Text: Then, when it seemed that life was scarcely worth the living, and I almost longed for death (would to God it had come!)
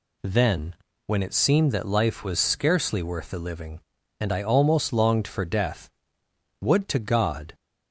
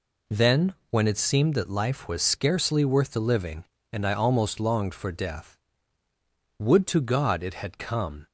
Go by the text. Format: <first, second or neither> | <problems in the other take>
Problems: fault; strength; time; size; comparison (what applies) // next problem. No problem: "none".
second | stops before "it had come"; at 7.5 s